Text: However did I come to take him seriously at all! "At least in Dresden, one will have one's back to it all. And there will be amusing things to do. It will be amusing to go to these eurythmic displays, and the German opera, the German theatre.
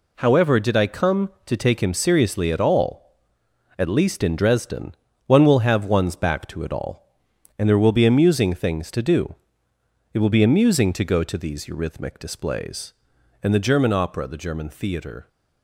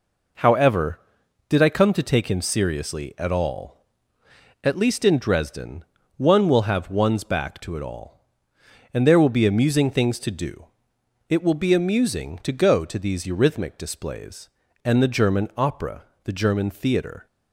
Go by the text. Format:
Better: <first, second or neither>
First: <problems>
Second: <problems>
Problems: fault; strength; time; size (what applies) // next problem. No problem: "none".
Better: neither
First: none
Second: none